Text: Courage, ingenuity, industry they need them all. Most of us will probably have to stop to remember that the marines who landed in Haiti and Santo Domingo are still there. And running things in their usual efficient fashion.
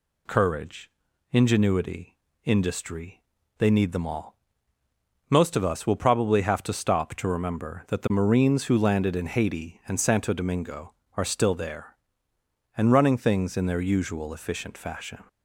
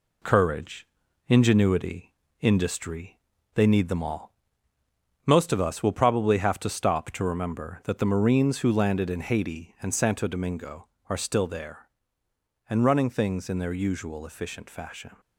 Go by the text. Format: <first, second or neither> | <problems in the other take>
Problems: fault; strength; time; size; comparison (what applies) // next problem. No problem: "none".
first | gets quieter; noticeable; throughout; 4 dB // pauses between "industry" and "they"; slight; at 3.1 s; 0.36 s long; slight in the first